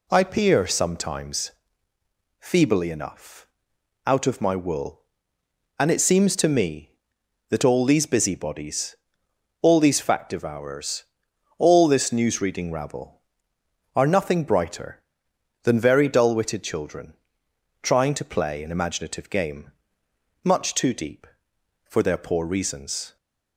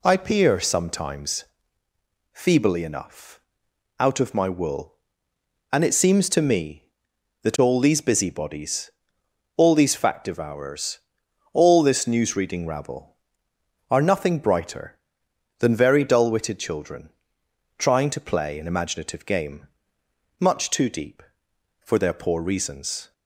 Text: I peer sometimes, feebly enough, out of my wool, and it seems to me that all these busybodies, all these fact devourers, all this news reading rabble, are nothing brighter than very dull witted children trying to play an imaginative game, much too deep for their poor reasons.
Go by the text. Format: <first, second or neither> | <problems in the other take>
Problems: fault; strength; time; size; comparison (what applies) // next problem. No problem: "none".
neither | pauses between "children" and "trying"; noticeable; the same in both